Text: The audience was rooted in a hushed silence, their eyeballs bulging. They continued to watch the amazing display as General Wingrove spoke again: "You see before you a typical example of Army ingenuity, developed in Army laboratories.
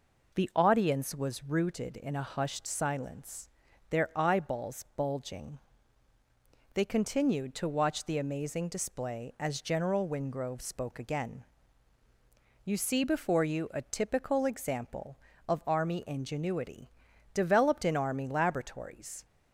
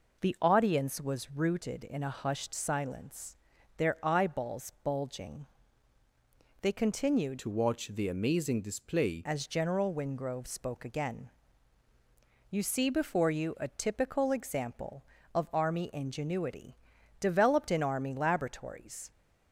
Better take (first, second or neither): first